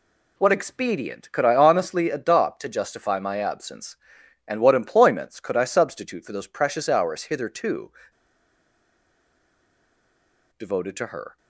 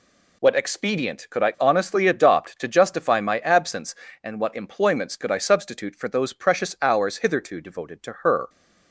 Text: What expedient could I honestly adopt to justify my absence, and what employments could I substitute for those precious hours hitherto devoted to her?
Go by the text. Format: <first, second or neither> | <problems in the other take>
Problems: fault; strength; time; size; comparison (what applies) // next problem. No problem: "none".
second | pauses between "hitherto" and "devoted"; strong; at 7.9 s; 2.6 s long